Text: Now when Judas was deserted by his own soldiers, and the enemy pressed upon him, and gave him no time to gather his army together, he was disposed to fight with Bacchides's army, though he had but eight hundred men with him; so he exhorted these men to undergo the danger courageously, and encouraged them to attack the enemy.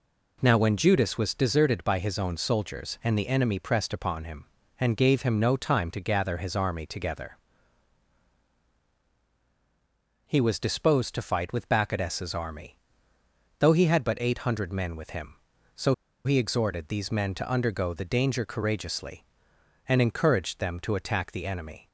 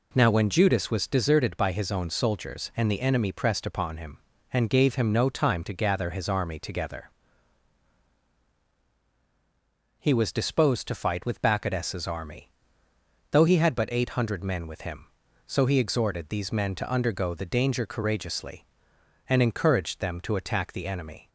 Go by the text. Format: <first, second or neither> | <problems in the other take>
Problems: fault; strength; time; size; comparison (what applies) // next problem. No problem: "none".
second | pauses between "so" and "he"; slight; at 15.9 s; 0.30 s long